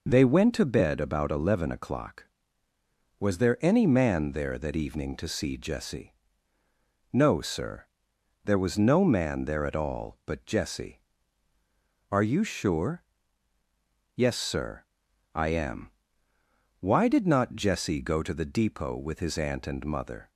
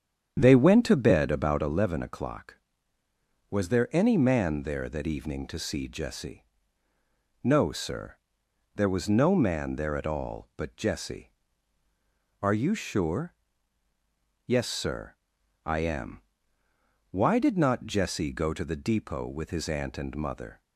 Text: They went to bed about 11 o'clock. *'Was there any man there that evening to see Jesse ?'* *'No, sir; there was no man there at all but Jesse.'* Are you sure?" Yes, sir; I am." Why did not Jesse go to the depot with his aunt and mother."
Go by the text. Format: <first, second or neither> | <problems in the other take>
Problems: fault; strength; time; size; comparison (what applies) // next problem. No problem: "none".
first | starts louder than the rest; strong; until 1.8 s; 8.5 dB